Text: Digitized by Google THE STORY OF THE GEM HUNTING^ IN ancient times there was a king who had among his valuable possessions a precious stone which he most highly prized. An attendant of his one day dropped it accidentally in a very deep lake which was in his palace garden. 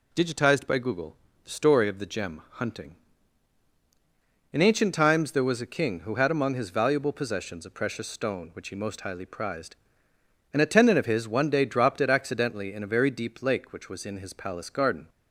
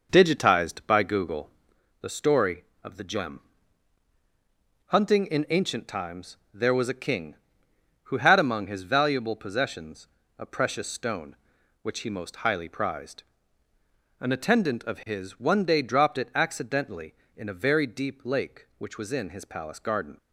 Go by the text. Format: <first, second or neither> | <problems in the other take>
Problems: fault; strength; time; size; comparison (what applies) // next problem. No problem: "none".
first | starts louder than the rest; noticeable; until 1.8 s; 5.5 dB // pauses between "Google" and "THE"; noticeable; at 1.5 s; 0.50 s long; slight in the first // pauses between "GEM" and "HUNTING"; strong; at 3.3 s; 1.4 s long // pauses between "times" and "there"; slight; at 6.3 s; 0.16 s long // pauses between "possessions" and "a"; slight; at 10.0 s; 0.28 s long